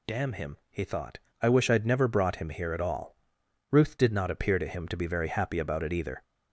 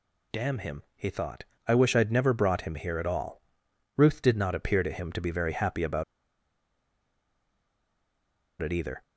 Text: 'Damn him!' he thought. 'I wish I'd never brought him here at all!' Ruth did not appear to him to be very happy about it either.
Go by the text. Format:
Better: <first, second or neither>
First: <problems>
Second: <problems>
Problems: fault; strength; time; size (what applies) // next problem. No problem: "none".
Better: first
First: none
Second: pauses between "about" and "it"; strong; at 6.0 s; 2.5 s long